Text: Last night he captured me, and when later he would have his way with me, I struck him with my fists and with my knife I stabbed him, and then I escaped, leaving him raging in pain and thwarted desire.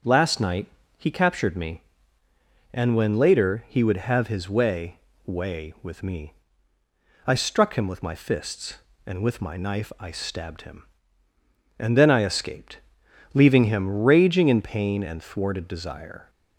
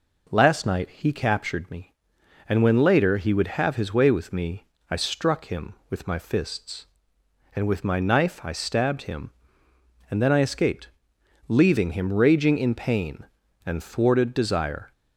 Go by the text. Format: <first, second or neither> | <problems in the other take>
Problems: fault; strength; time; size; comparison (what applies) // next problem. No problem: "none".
second | starts louder than the rest; until 1.3 s; 7 dB // pauses between "night" and "he"; slight; at 0.6 s; 0.30 s long // says "way" twice; at 5.2 s